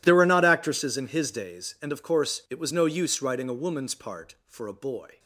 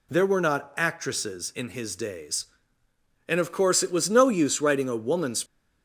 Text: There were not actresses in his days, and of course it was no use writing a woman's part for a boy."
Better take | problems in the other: first | stops before "part for a boy"; at 5.4 s

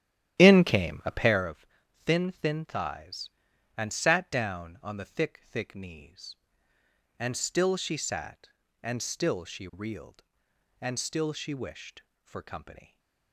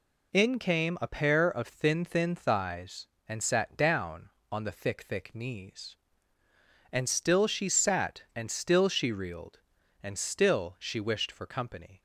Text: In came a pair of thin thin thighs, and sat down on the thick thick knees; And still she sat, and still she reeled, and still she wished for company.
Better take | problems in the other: second | starts louder than the rest; strong; until 1.5 s; 11.5 dB // pauses between "of" and "thin"; at 1.6 s; 0.42 s long

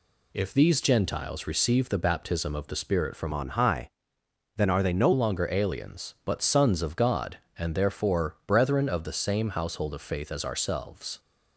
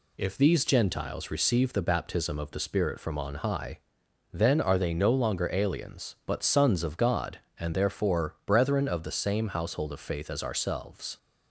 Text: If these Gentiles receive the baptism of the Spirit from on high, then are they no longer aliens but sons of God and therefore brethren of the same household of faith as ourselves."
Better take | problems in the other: second | changes voice from "on" to "no"; from 3.3 to 5.1 s; 1.8 s long

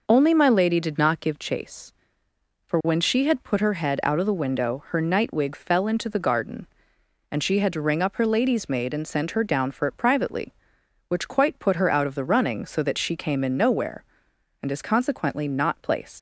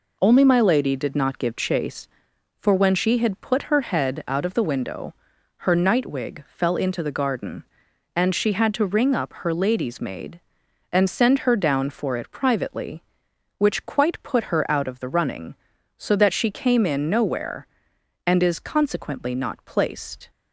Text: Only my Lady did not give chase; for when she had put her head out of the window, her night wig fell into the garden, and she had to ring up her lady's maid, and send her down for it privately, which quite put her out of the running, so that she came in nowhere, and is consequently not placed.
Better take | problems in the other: second | leaves "placed" unfinished; at 16.1 s; 120 ms

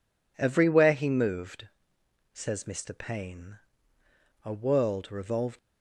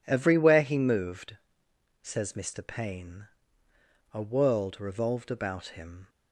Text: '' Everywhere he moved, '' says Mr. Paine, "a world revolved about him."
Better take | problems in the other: second | stops before "about him"; at 5.5 s

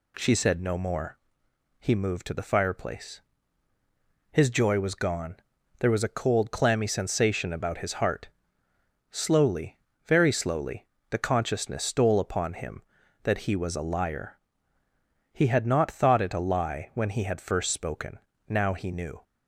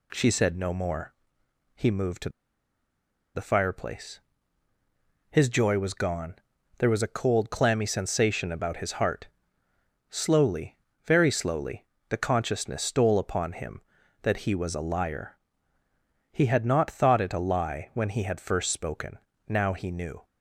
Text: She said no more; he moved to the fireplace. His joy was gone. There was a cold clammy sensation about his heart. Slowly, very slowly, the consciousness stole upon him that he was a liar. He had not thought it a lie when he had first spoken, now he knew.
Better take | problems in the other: first | pauses between "to" and "the"; at 2.2 s; 1.0 s long

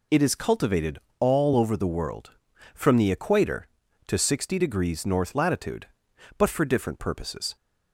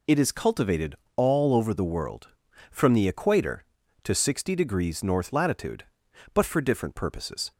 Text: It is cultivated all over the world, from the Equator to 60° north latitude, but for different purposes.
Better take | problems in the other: neither | pauses between "cultivated" and "all"; slight; the same in both

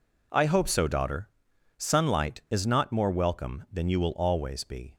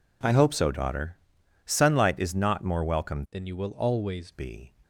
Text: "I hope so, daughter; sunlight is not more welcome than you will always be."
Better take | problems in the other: first | changes voice from "than" to "always"; from 3.3 to 4.3 s; 1.0 s long

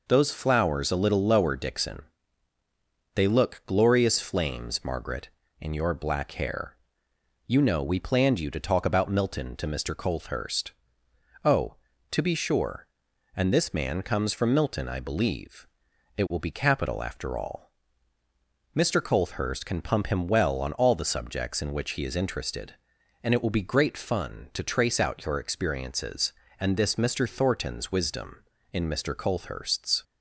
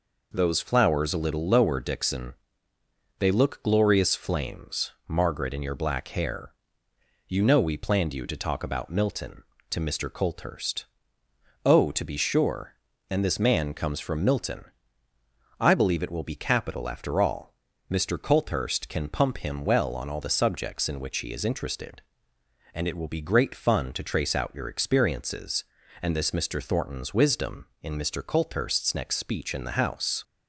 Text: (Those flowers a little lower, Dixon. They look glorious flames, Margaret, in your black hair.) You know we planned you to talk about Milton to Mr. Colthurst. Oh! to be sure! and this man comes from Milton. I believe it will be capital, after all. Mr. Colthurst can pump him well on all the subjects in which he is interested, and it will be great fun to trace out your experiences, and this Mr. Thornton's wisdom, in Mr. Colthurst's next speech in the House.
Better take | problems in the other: second | pauses between "believe" and "it"; noticeable; at 15.6 s; 0.52 s long // stops before "next speech in the House"; at 30.0 s

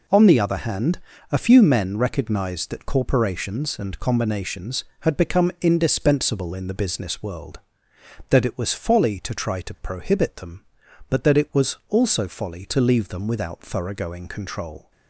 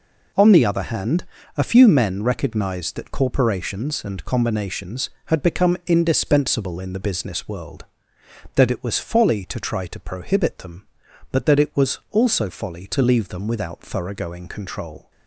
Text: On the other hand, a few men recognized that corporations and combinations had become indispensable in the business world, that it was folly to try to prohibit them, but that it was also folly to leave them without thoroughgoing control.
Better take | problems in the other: neither | none

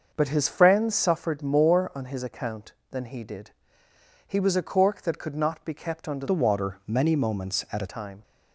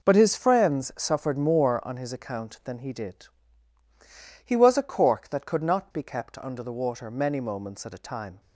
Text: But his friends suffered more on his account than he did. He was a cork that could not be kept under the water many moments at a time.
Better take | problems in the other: second | starts louder than the rest; until 1.1 s; 6 dB // changes voice from "the" to "a"; from 6.2 to 7.8 s; 1.6 s long

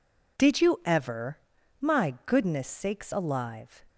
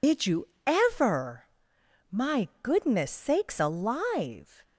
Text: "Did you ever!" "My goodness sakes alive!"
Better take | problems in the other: first | loses the start of "Did"; at 0.0 s; 70 ms // pauses between "you" and "ever"; slight; at 0.4 s; 0.18 s long

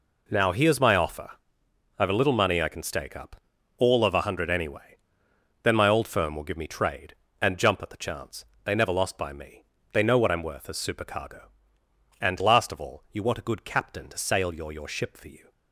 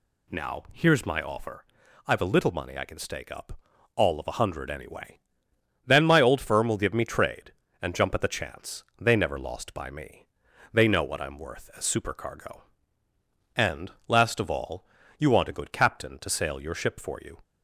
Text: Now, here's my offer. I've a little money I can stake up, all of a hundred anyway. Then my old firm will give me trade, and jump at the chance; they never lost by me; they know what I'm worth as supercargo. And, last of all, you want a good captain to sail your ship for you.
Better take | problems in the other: second | says "your" twice; at 14.7 s

